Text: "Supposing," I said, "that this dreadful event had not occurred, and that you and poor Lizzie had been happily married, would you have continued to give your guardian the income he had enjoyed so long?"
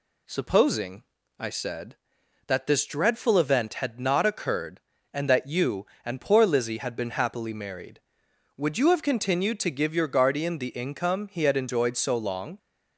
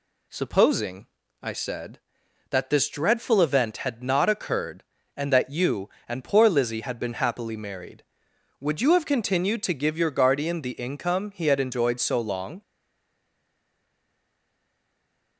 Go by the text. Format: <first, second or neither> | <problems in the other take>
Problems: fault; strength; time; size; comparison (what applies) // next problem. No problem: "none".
first | stays silent after the last word; strong; from 12.6 s on; 2.7 s long